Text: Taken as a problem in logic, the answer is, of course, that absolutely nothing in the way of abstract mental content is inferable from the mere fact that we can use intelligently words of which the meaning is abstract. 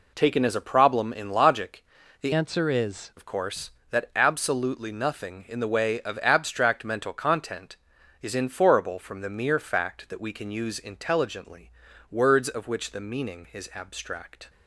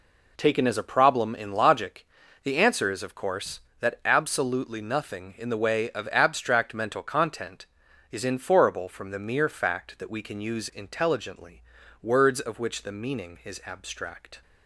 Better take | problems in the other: second | changes voice from "answer" to "is"; from 2.3 to 3.1 s; 0.8 s long // pauses between "intelligently" and "words"; at 11.6 s; 0.40 s long; also in the second

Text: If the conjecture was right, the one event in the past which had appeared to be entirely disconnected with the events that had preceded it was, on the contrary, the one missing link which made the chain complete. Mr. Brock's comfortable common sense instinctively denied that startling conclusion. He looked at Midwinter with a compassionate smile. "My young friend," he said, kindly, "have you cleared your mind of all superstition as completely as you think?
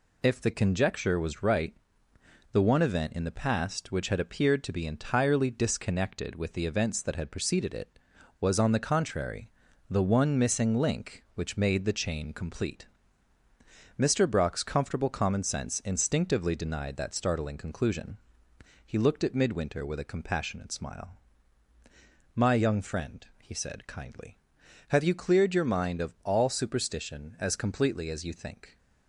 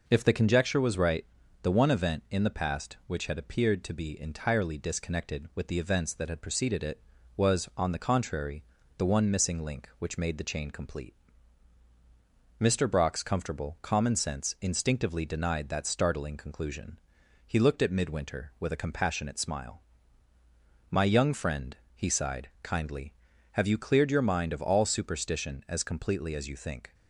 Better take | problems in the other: first | says "sighed" for "said"; at 22.0 s

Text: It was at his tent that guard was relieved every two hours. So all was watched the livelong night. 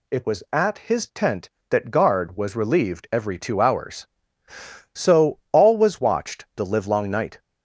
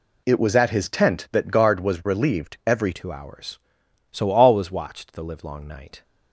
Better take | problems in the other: first | changes voice at "two"; from 2.9 s on; 3.1 s long

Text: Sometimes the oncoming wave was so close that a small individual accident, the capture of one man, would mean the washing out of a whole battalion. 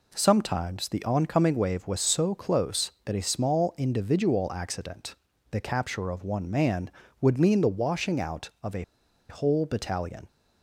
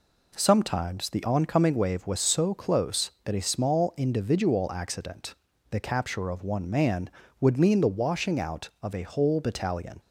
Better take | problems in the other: second | pauses between "a" and "whole"; noticeable; at 8.8 s; 0.46 s long

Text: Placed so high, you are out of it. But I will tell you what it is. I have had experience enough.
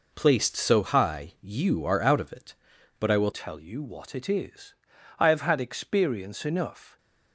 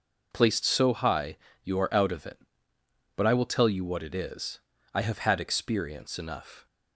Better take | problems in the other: second | changes voice at "tell"; from 3.3 s on; 3.6 s long

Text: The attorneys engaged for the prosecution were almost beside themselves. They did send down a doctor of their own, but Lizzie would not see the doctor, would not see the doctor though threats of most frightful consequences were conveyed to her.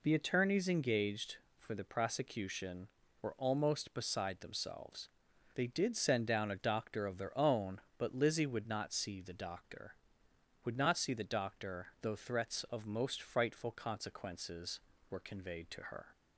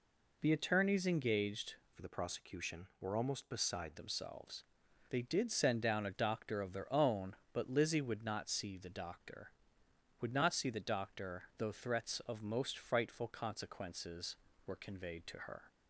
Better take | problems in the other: first | changes voice from "for" to "beside"; from 1.9 to 3.9 s; 2.0 s long

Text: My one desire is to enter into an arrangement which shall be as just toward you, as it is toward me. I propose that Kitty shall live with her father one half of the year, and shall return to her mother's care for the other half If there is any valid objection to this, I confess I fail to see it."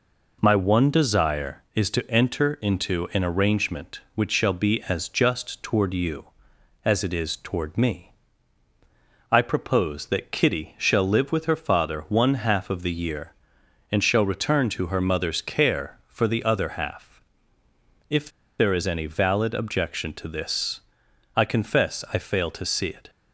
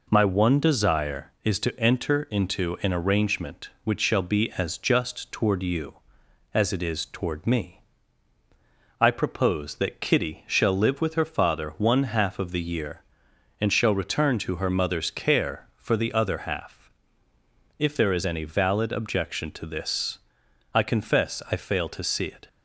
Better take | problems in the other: second | pauses between "half" and "If"; noticeable; at 17.2 s; 0.88 s long; noticeable in the second // pauses between "If" and "there"; slight; at 18.2 s; 0.29 s long

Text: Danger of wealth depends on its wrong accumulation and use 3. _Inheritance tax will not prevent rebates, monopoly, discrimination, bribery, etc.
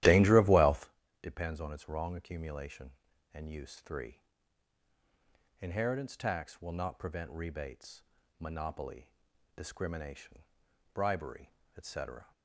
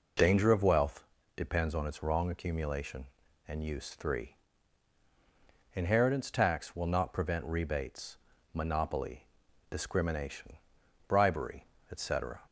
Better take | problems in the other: second | starts louder than the rest; strong; until 1.0 s; 14 dB // pauses between "wealth" and "depends"; slight; at 0.8 s; 0.32 s long; slight in the second

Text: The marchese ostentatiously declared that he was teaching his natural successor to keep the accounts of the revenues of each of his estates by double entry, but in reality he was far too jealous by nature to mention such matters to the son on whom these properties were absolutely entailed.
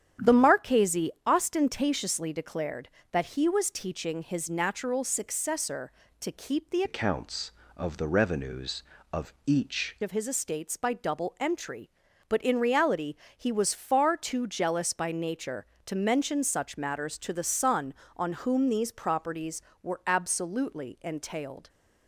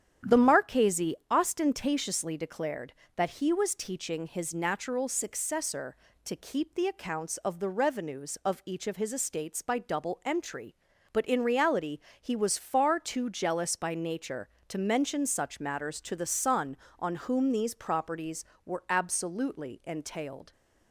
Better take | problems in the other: second | starts louder than the rest; strong; until 1.3 s; 9.5 dB; strong in the second // changes voice from "accounts" to "each"; from 6.8 to 9.9 s; 3.1 s long // pauses between "reality" and "he"; slight; at 13.1 s; 0.22 s long; slight in the second

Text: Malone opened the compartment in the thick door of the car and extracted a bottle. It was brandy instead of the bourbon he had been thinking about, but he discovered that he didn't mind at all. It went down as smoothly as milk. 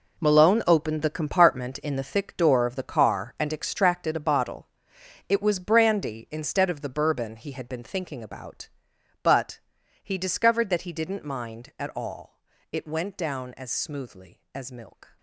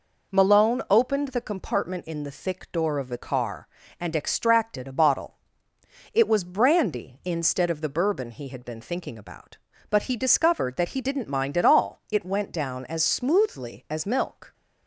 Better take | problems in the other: second | gets quieter; strong; throughout; 13.5 dB // pauses between "but" and "he"; at 9.5 s; 0.44 s long

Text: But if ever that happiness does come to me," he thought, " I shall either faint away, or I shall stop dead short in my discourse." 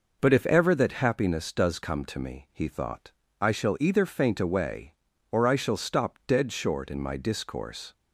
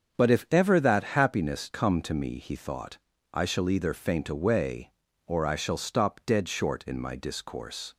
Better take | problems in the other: first | starts louder than the rest; strong; until 1.2 s; 7.5 dB // skips "does"; at 1.7 s

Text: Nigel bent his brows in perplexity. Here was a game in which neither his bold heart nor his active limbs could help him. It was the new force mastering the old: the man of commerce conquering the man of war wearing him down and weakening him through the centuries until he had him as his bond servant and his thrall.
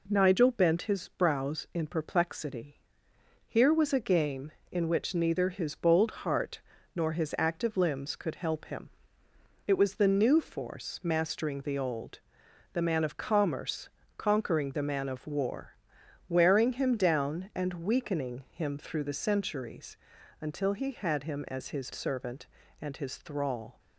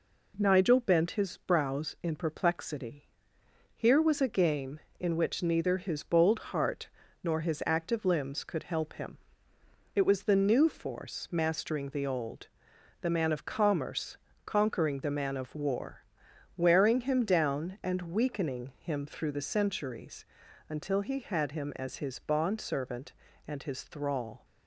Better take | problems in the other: second | pauses between "heart" and "nor"; slight; at 6.6 s; 0.34 s long; slight in the second // pauses between "commerce" and "conquering"; slight; at 13.8 s; 0.28 s long; slight in the second // pauses between "war" and "wearing"; noticeable; at 15.7 s; 0.54 s long; noticeable in the second // pauses between "centuries" and "until"; at 19.9 s; 0.44 s long; also in the second // skips "bond"; at 21.9 s

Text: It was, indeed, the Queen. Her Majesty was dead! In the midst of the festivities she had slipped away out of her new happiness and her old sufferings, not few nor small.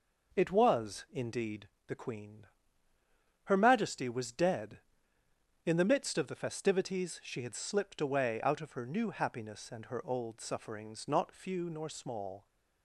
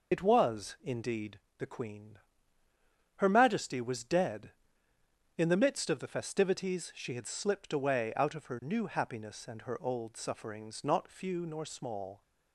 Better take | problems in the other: first | loses the start of "It"; at 0.1 s; 85 ms

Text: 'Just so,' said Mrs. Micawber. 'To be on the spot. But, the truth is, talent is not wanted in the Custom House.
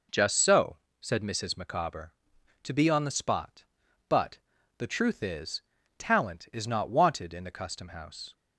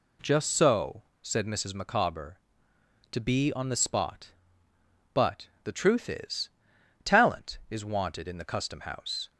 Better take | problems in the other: first | skips "not"; at 7.8 s

